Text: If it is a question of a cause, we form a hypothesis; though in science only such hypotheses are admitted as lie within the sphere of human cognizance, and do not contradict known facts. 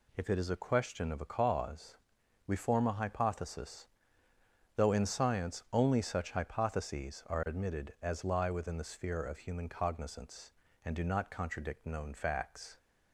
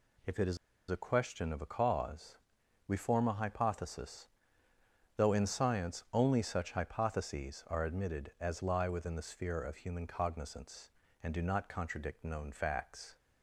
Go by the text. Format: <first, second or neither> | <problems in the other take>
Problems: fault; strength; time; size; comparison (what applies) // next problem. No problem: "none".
first | pauses between "is" and "a"; slight; at 0.5 s; 0.33 s long